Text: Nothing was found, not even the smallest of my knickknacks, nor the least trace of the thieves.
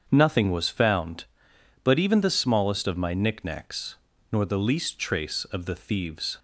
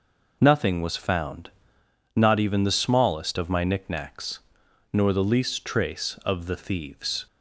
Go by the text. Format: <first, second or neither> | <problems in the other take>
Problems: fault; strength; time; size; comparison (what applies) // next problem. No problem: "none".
second | starts louder than the rest; strong; until 1.1 s; 7.5 dB // says "but" for "not"; at 1.8 s